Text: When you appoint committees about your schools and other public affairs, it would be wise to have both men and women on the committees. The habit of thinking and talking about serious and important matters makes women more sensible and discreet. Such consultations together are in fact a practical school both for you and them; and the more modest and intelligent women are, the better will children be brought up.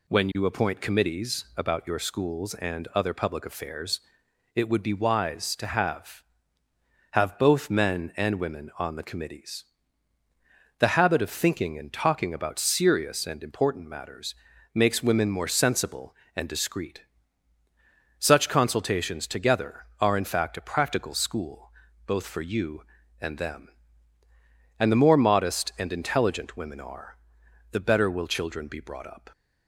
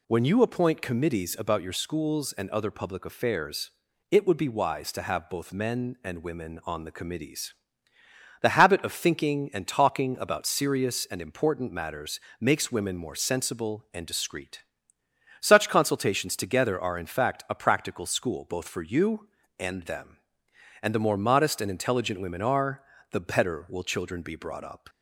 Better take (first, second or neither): second